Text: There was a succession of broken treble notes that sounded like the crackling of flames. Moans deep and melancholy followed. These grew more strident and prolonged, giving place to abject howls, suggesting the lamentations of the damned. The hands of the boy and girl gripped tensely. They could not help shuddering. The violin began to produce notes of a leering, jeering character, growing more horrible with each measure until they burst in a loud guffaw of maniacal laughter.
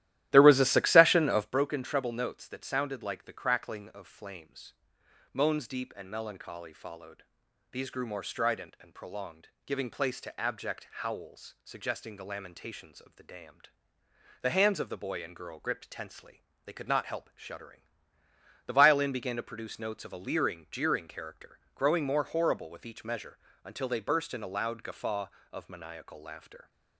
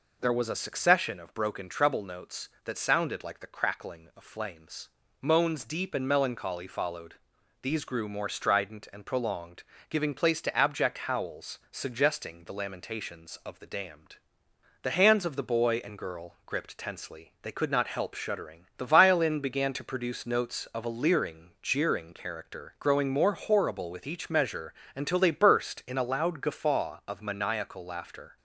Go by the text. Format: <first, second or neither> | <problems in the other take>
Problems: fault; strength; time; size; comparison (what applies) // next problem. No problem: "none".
second | starts louder than the rest; strong; until 1.6 s; 14 dB // pauses between "measure" and "until"; slight; at 23.3 s; 0.26 s long; slight in the second